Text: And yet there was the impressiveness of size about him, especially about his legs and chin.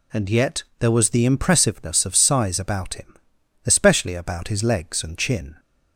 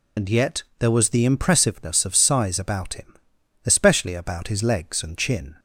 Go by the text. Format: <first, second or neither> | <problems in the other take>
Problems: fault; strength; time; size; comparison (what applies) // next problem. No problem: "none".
first | loses the start of "And"; at 0.1 s; 50 ms // pauses between "yet" and "there"; slight; at 0.6 s; 0.16 s long; slight in the first